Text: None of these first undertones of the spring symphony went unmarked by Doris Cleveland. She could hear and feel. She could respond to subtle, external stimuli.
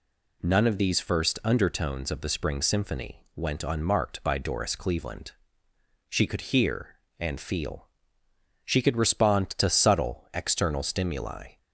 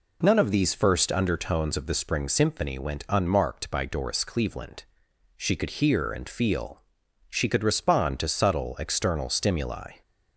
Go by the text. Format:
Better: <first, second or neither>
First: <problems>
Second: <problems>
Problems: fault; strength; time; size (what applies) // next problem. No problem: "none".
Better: neither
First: none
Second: none